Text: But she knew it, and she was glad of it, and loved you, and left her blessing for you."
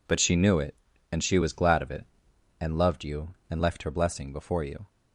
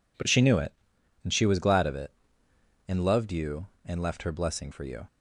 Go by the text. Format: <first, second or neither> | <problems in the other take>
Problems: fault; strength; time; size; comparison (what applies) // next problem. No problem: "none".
second | says "before" for "for"; at 4.3 s